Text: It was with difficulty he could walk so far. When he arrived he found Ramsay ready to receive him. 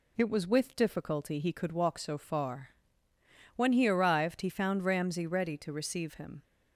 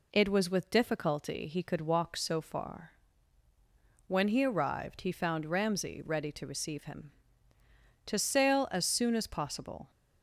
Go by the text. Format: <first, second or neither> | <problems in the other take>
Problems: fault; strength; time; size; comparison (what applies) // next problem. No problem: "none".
first | goes on to say "To sail as soon as possible"; strong; from 8.0 s on; 1.8 s long